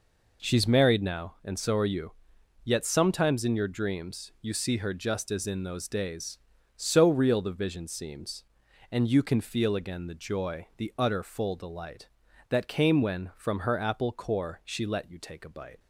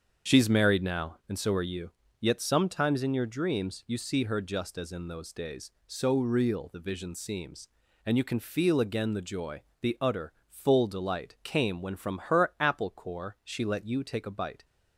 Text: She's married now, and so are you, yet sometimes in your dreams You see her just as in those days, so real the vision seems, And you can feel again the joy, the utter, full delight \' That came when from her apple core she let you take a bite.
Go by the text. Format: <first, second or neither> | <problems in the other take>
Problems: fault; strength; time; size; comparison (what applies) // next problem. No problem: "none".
first | starts louder than the rest; until 1.3 s; 7 dB // skips "That"; at 11.4 s